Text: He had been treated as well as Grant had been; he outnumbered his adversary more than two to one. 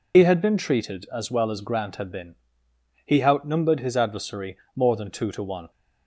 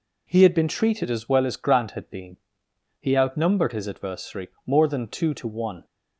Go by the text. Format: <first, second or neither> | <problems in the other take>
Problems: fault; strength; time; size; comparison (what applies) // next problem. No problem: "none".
second | loses the start of "He"; at 0.1 s; 90 ms // pauses between "adversary" and "more"; slight; at 4.5 s; 0.18 s long; slight in the second